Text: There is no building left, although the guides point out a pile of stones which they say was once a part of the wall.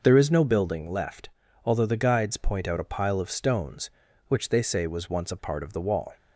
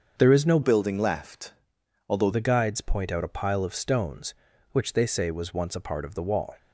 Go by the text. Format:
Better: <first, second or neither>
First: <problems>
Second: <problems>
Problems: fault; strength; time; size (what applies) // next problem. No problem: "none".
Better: first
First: none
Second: starts louder than the rest; until 1.2 s; 6.5 dB // changes voice from "building" to "although"; from 0.6 to 2.3 s; 1.7 s long